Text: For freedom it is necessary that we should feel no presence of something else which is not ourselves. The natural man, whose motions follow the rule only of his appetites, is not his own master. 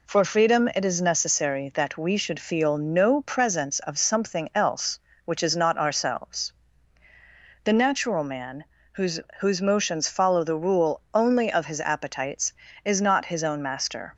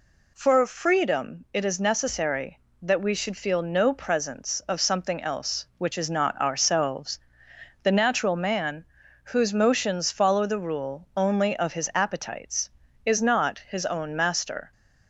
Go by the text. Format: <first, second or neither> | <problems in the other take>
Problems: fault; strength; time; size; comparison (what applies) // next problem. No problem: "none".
second | says "whose" twice; at 9.4 s